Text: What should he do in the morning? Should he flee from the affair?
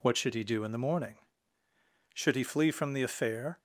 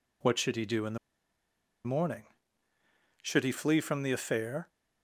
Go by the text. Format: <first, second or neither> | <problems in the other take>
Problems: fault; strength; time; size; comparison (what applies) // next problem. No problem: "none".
first | pauses between "the" and "morning"; noticeable; at 0.9 s; 0.88 s long